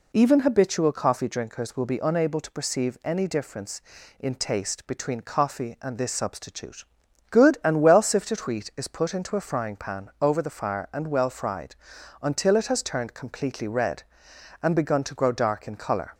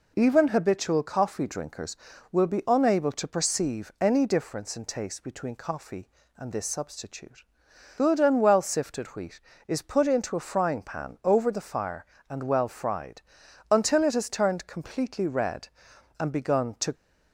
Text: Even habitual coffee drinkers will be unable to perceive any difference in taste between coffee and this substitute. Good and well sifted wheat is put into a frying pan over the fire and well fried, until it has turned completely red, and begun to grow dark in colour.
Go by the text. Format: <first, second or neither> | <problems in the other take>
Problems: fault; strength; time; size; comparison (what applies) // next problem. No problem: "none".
first | stops before "grow dark in colour"; at 16.9 s